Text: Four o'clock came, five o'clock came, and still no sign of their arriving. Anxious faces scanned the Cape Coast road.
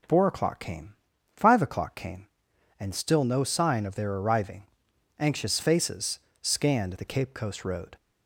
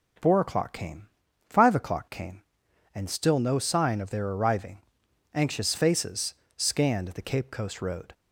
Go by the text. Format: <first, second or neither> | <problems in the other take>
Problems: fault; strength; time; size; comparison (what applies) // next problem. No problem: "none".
neither | pauses between "faces" and "scanned"; slight; the same in both